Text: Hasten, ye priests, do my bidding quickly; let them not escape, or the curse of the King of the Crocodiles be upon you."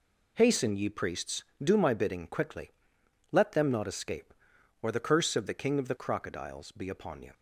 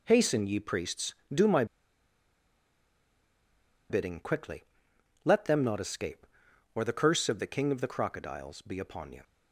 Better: first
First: none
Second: pauses between "my" and "bidding"; strong; at 1.6 s; 2.2 s long

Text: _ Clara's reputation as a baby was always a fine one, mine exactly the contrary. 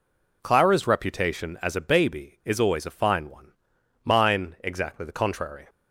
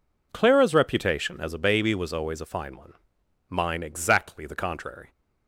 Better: second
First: says "is" for "was"; at 2.4 s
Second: none

